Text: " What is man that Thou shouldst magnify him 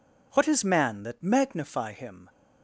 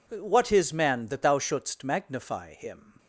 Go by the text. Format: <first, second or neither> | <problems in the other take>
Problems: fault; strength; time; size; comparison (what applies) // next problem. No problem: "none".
second | skips "Thou shouldst"; at 1.2 s